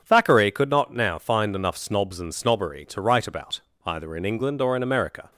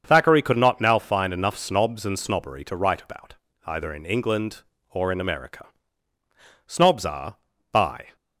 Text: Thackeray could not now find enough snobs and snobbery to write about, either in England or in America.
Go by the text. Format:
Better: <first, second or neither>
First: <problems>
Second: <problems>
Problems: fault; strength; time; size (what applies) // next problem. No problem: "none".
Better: first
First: none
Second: starts louder than the rest; strong; until 1.0 s; 7 dB // goes on to say "Snobs are by"; from 6.6 s on; 1.4 s long